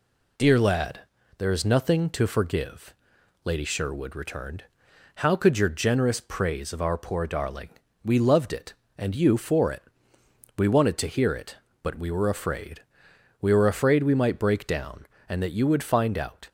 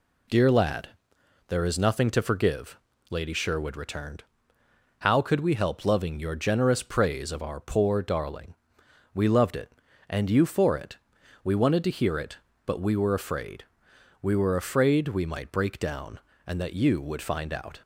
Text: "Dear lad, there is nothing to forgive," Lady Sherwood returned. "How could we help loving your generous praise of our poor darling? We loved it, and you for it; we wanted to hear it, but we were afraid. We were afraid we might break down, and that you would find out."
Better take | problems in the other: second | skips "we help loving"; at 5.5 s

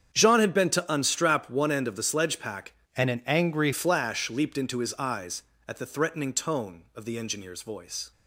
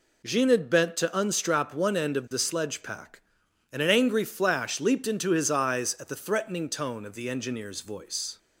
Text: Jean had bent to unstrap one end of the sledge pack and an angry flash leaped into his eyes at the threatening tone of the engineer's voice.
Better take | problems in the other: second | starts louder than the rest; strong; until 1.1 s; 8 dB // changes voice from "and" to "angry"; from 2.9 to 3.7 s; 0.8 s long

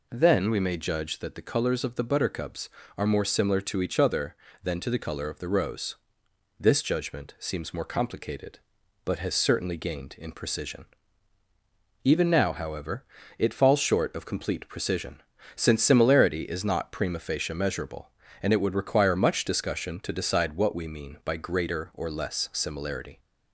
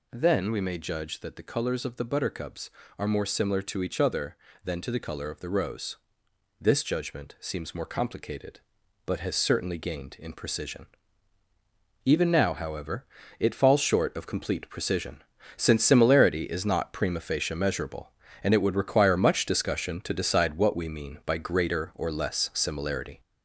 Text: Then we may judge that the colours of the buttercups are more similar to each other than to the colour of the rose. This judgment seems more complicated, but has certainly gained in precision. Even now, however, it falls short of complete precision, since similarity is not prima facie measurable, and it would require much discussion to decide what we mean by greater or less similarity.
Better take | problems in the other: first | gets louder; noticeable; throughout; 5 dB

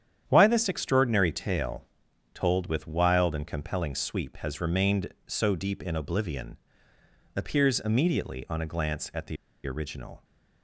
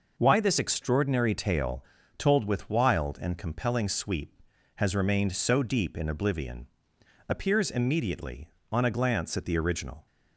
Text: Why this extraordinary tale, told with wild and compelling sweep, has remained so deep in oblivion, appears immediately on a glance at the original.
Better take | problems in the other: second | starts louder than the rest; strong; until 1.2 s; 9.5 dB // pauses between "the" and "original"; slight; at 9.3 s; 0.31 s long

